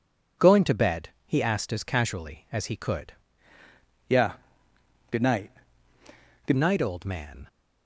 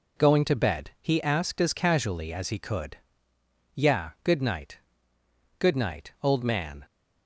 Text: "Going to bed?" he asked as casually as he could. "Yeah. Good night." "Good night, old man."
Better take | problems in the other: second | changes voice from "Yeah" to "Good"; from 4.0 to 6.5 s; 2.5 s long

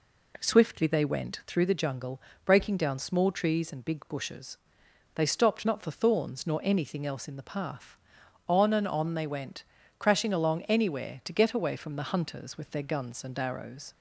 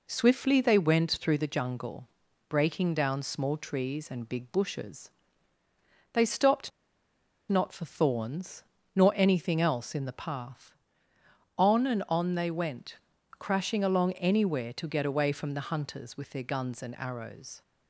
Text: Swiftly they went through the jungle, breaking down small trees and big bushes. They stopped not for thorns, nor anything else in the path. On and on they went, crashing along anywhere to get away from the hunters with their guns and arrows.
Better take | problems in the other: first | pauses between "stopped" and "not"; noticeable; at 6.7 s; 0.79 s long

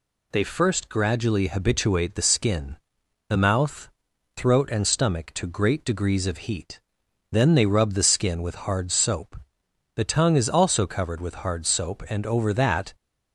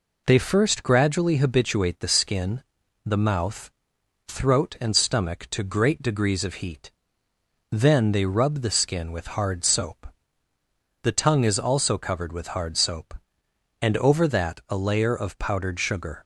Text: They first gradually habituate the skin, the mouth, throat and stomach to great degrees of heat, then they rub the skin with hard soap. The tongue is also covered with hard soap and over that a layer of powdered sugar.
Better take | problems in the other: second | stops before "a layer of powdered sugar"; at 12.9 s

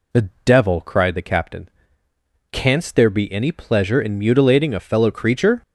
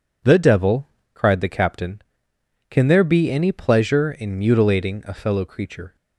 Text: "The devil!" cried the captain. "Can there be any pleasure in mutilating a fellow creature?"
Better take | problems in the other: second | pauses between "The" and "devil"; slight; at 0.2 s; 0.16 s long // says "Canst" for "Can"; at 2.4 s

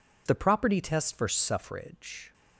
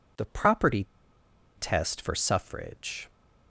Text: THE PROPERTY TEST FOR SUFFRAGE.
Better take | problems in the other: first | pauses between "PROPERTY" and "TEST"; noticeable; at 0.8 s; 0.72 s long

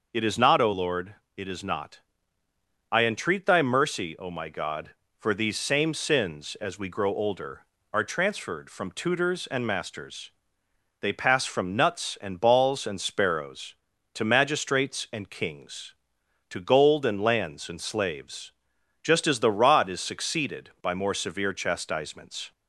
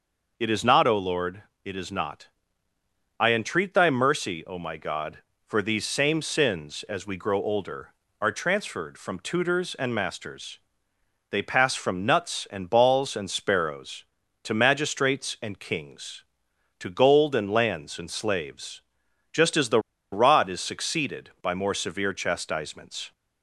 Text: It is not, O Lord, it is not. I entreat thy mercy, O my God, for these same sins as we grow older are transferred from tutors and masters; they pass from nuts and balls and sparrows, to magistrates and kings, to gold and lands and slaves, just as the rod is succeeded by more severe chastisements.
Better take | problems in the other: first | pauses between "the" and "rod"; slight; at 19.7 s; 0.33 s long

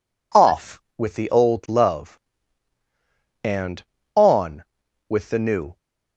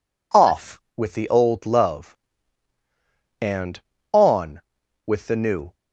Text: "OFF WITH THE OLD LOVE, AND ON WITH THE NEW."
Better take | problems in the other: neither | none

